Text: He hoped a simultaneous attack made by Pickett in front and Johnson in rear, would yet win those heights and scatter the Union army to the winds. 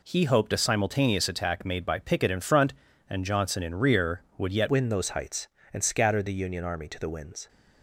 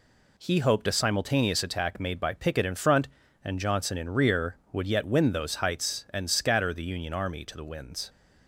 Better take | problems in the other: second | changes voice at "win"; from 4.6 s on; 2.8 s long

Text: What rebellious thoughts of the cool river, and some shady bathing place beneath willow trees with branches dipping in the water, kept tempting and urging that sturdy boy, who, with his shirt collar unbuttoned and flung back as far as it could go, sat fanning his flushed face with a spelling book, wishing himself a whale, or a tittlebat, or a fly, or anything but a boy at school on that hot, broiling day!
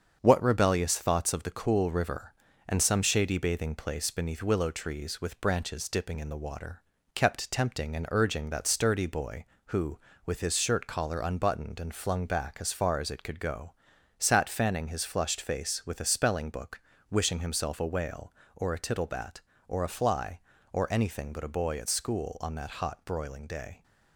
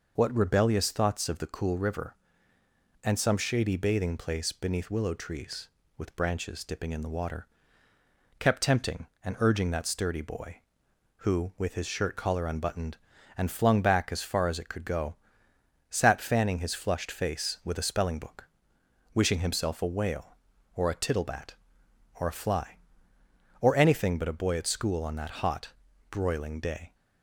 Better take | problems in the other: second | gets quieter; noticeable; throughout; 4.5 dB

